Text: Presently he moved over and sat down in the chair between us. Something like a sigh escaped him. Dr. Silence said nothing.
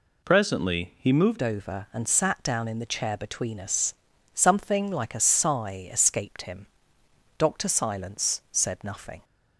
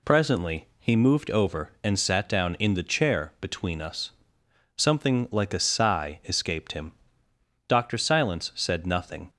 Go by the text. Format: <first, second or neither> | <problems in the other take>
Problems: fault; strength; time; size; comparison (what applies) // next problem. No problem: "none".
second | changes voice at "over"; from 1.4 s on; 7.8 s long